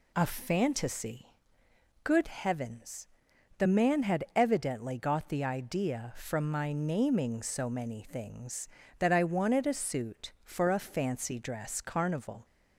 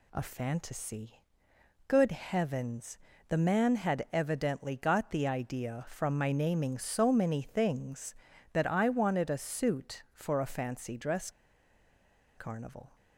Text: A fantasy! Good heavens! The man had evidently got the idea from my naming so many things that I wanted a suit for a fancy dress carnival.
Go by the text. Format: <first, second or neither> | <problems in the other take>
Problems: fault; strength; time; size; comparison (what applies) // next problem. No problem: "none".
first | pauses between "dress" and "carnival"; at 11.2 s; 1.0 s long